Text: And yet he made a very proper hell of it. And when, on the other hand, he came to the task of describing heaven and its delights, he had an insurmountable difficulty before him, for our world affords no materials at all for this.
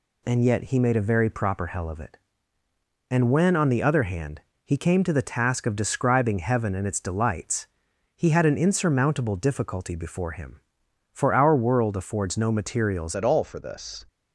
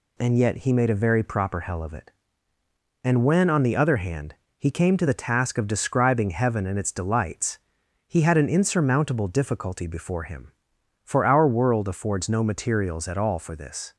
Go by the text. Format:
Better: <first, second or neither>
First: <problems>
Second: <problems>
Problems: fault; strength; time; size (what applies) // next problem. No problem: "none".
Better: second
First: changes voice at "at"; from 13.1 s on; 0.9 s long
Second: none